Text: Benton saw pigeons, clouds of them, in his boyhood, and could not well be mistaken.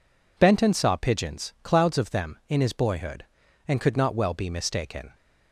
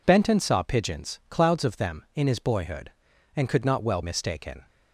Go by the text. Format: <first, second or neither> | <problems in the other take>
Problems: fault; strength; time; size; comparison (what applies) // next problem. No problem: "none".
first | skips "be"; at 4.0 s